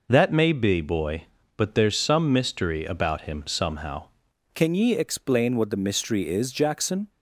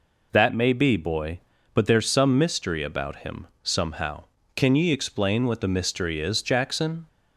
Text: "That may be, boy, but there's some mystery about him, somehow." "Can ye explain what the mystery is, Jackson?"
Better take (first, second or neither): second